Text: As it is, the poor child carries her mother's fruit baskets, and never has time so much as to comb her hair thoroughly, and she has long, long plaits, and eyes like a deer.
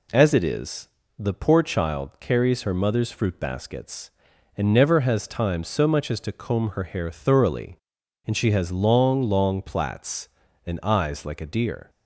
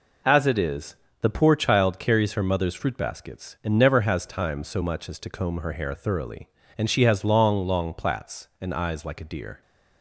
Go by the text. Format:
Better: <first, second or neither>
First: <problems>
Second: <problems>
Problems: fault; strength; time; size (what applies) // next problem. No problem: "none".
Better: neither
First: none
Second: none